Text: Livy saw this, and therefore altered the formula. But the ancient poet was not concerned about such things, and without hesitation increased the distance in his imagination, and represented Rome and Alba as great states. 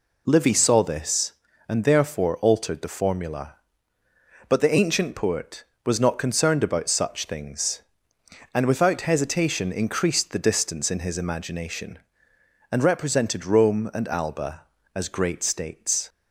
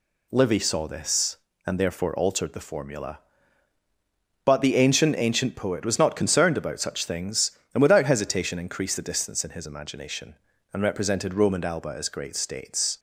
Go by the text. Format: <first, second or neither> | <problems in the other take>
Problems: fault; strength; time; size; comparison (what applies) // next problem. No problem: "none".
first | says "ancient" twice; at 5.1 s